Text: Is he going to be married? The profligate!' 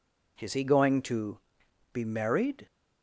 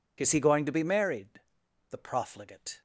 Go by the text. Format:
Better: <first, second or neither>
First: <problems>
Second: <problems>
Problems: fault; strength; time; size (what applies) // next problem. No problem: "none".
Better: second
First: pauses between "to" and "be"; noticeable; at 1.3 s; 0.56 s long // stops before "The profligate"; at 2.6 s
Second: none